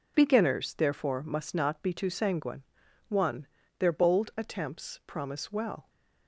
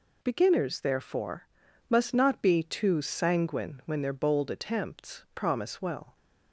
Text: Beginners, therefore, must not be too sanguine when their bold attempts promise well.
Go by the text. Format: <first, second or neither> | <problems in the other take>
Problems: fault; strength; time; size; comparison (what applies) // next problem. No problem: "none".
second | says "one" for "when"; at 3.0 s